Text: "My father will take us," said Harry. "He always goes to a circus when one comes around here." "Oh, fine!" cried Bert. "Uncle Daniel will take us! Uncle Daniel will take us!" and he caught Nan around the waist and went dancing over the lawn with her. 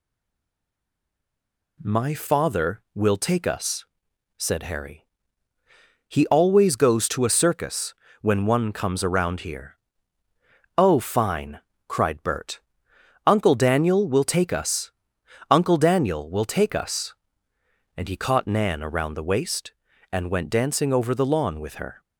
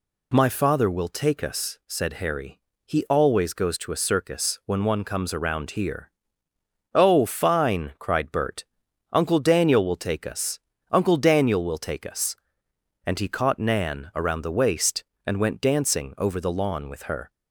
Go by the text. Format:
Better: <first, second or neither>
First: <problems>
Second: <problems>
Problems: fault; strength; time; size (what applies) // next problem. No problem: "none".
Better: second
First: stays silent before the first word; noticeable; until 1.7 s; 1.7 s long // pauses between "circus" and "when"; slight; at 7.9 s; 0.26 s long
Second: none